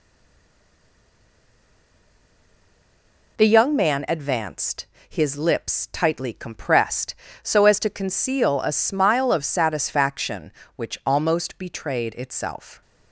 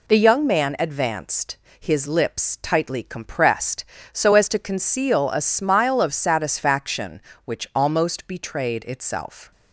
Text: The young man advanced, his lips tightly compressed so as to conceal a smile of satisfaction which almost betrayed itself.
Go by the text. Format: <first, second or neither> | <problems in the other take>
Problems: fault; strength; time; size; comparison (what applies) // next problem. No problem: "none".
second | stays silent before the first word; strong; until 3.3 s; 3.3 s long